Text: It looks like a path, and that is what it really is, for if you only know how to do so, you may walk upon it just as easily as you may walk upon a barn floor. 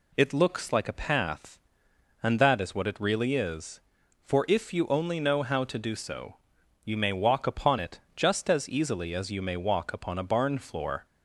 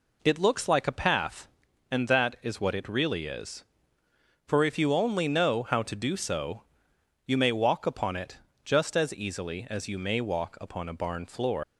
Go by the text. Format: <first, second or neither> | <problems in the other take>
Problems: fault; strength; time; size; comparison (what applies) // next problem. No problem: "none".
first | pauses between "it" and "just"; slight; at 8.3 s; 0.26 s long; slight in the first // leaves "floor" unfinished; at 11.6 s; 85 ms